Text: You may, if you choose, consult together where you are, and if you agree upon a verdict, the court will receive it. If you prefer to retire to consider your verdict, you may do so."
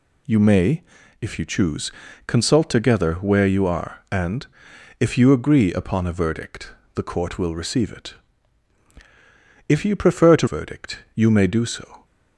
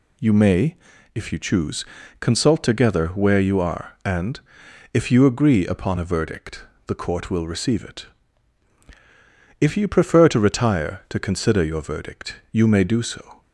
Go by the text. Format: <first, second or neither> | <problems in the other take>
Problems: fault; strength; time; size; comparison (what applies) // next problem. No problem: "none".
second | pauses between "and" and "if"; noticeable; at 4.4 s; 0.54 s long; noticeable in the second // skips "retire to consider your"; at 10.4 s